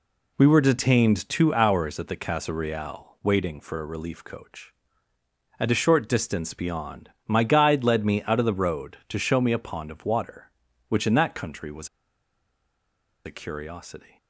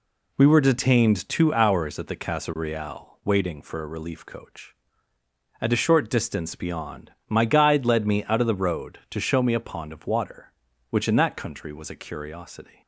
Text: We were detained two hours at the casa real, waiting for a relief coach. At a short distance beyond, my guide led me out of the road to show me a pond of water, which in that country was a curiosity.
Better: second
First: pauses between "was" and "a"; strong; at 11.8 s; 1.3 s long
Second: none

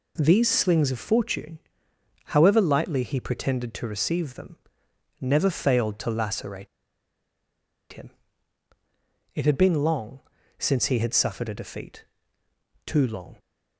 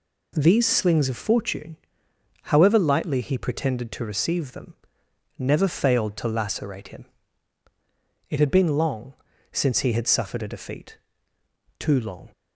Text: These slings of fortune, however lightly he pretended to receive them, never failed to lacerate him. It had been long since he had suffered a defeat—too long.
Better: second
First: pauses between "lacerate" and "him"; strong; at 6.6 s; 1.2 s long // pauses between "long" and "since"; at 10.1 s; 0.38 s long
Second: pauses between "long" and "since"; at 9.1 s; 0.38 s long

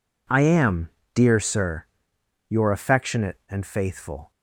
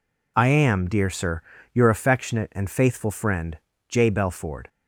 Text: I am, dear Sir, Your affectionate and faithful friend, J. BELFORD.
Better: second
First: stops before "friend J BELFORD"; at 4.3 s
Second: none

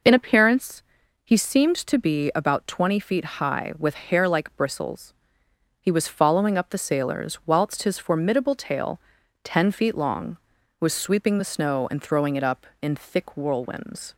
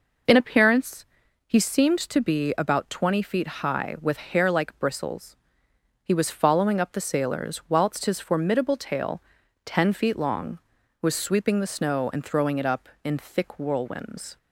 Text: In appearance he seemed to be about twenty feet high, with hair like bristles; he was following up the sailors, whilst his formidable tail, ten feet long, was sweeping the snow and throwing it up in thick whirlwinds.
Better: neither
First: pauses between "appearance" and "he"; at 0.8 s; 0.44 s long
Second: pauses between "appearance" and "he"; at 1.0 s; 0.44 s long

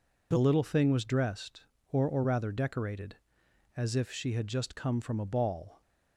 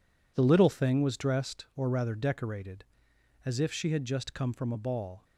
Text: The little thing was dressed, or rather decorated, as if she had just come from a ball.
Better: second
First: says "or" twice; at 2.0 s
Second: none

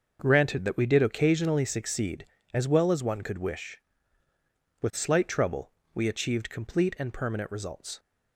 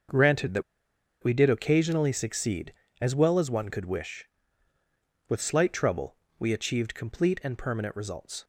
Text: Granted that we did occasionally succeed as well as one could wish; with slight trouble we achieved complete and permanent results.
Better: first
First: starts louder than the rest; noticeable; until 1.2 s; 6 dB // pauses between "trouble" and "we"; slight; at 5.7 s; 0.20 s long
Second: starts louder than the rest; until 1.7 s; 6.5 dB // pauses between "that" and "we"; noticeable; at 0.6 s; 0.60 s long // pauses between "trouble" and "we"; slight; at 6.1 s; 0.20 s long

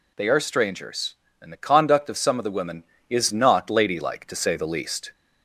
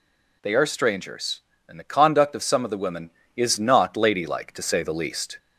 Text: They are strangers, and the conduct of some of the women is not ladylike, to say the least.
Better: neither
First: none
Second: none

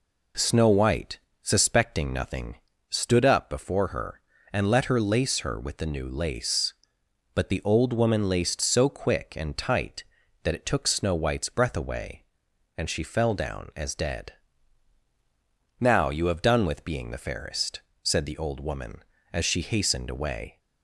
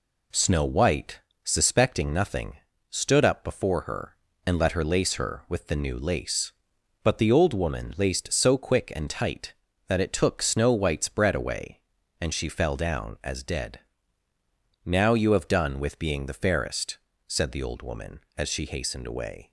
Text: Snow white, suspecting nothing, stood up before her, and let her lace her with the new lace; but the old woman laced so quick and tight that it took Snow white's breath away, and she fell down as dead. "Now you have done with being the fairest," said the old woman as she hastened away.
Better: first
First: none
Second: says "bread" for "breath"; at 11.0 s

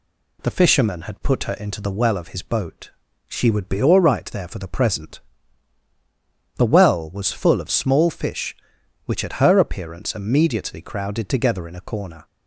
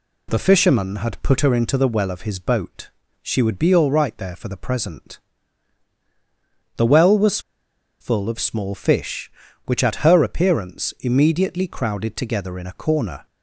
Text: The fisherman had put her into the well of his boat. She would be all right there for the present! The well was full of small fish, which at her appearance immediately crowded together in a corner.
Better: first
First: none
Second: pauses between "was" and "full"; noticeable; at 7.3 s; 0.61 s long

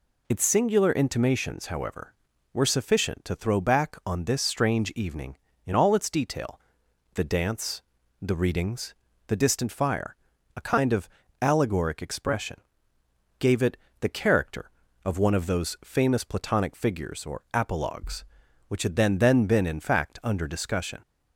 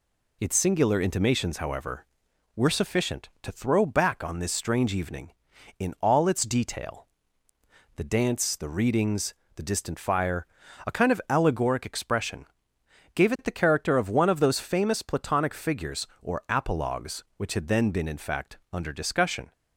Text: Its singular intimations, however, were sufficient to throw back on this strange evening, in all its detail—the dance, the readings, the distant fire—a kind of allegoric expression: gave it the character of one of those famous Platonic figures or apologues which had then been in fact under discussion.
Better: second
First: pauses between "of" and "allegoric"; slight; at 11.0 s; 0.32 s long // pauses between "it" and "the"; slight; at 13.7 s; 0.24 s long // says "then" twice; at 19.1 s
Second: none

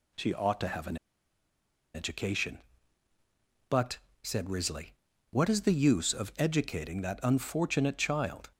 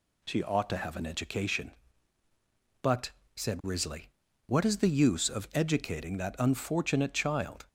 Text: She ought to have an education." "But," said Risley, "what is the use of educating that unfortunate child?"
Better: second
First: pauses between "an" and "education"; at 0.9 s; 0.99 s long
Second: none

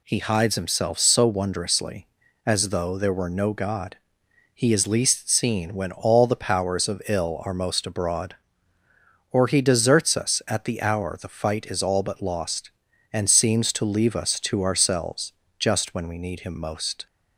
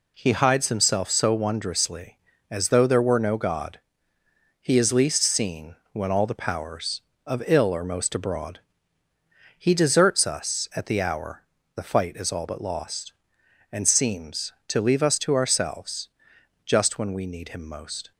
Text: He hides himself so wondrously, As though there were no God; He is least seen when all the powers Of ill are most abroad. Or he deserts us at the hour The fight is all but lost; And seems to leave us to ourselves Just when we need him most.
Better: first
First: pauses between "ourselves" and "Just"; slight; at 15.3 s; 0.26 s long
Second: pauses between "seen" and "when"; slight; at 5.7 s; 0.16 s long // skips "Or"; at 9.1 s // pauses between "hour" and "The"; slight; at 11.4 s; 0.32 s long // pauses between "ourselves" and "Just"; noticeable; at 16.0 s; 0.56 s long

